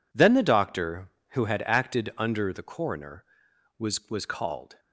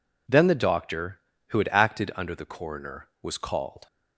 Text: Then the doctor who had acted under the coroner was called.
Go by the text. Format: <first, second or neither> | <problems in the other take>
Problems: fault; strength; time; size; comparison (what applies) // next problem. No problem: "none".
second | says "was" twice; at 4.0 s